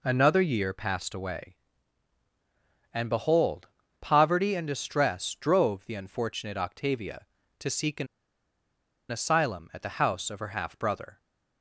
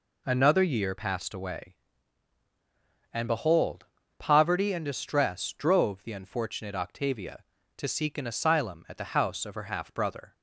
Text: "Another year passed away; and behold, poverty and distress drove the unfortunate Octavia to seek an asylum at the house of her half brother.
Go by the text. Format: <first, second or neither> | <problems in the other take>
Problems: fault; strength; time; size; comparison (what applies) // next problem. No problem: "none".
second | pauses between "an" and "asylum"; at 8.0 s; 1.0 s long